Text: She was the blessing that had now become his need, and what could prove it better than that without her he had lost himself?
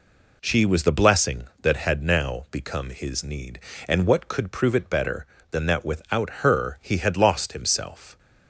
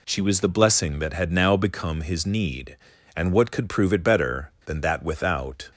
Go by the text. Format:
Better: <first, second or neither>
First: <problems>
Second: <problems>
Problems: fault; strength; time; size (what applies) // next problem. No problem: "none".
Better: first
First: none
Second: stops before "her he had lost himself"; at 5.7 s